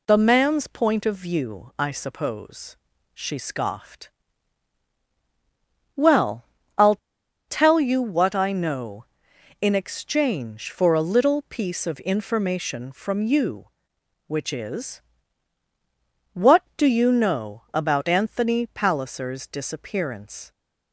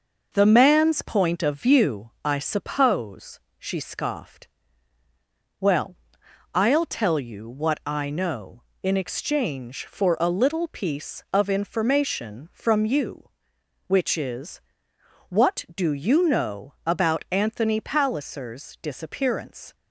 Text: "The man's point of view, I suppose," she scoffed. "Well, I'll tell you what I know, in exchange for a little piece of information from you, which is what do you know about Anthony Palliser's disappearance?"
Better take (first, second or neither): second